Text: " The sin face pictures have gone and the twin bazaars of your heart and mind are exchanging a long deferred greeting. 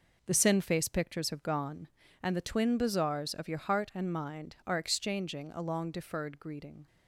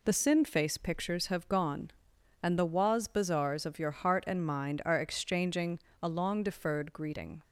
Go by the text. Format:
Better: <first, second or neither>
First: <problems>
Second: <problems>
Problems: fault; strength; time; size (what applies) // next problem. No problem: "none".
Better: first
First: none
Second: says "waz" for "twin"; at 2.6 s // pauses between "exchanging" and "a"; slight; at 5.7 s; 0.24 s long